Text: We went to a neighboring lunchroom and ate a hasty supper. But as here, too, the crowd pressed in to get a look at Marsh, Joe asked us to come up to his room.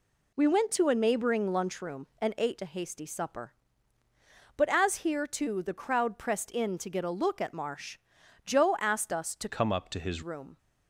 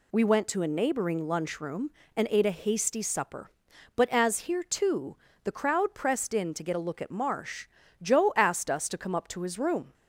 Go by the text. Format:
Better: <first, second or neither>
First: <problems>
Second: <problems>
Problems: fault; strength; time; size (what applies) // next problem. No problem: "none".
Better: second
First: changes voice from "come" to "his"; from 9.4 to 10.2 s; 0.8 s long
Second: none